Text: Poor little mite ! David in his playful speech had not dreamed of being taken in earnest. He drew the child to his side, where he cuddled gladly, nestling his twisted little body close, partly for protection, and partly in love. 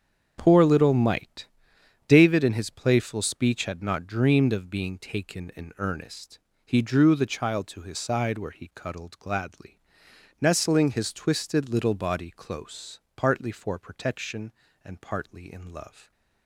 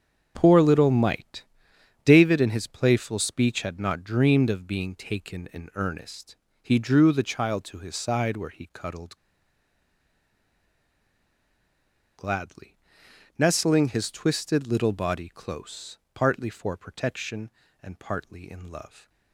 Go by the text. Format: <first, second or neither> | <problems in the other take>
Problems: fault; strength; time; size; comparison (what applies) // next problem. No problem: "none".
first | starts louder than the rest; strong; until 1.3 s; 7.5 dB; strong in the first // pauses between "cuddled" and "gladly"; strong; at 9.1 s; 3.0 s long